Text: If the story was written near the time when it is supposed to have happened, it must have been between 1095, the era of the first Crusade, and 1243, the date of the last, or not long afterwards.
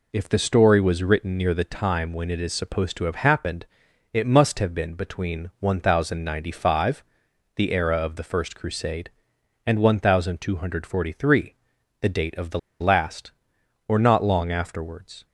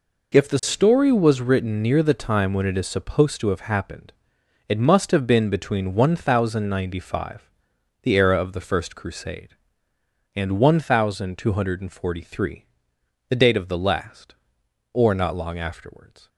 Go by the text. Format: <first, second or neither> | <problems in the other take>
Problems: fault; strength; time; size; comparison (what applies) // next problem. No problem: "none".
second | pauses between "the" and "last"; slight; at 12.5 s; 0.21 s long